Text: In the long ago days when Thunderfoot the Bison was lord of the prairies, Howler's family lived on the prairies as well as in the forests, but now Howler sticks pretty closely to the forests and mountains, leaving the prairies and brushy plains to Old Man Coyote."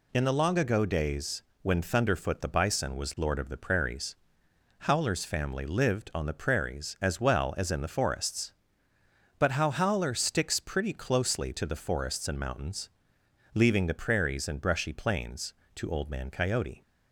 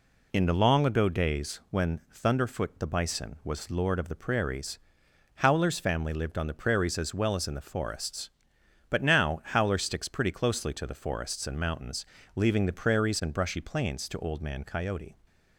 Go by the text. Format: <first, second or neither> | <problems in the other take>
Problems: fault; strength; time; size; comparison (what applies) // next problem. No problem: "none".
second | pauses between "days" and "when"; slight; at 1.4 s; 0.18 s long // says "how" for "now"; at 9.5 s